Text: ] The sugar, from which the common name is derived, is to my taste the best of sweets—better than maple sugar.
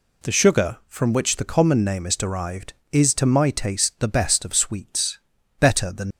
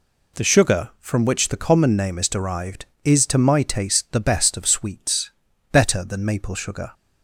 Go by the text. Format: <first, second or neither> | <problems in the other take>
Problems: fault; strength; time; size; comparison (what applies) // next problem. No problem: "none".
second | stops before "maple sugar"; at 6.1 s